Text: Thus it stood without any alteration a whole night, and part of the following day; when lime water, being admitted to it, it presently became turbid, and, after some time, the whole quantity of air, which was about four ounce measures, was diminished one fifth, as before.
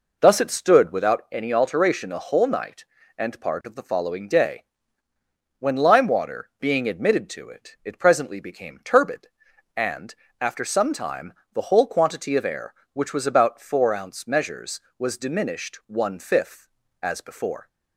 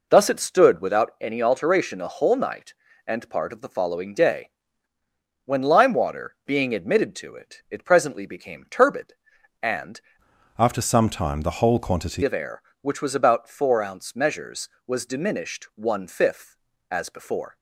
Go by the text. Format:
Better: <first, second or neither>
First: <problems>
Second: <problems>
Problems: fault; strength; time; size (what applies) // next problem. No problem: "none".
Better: first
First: none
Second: changes voice from "after" to "quantity"; from 10.5 to 12.2 s; 1.7 s long